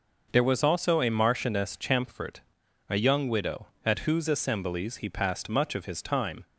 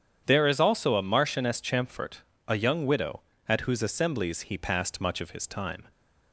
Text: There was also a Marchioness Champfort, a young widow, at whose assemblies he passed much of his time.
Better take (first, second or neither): first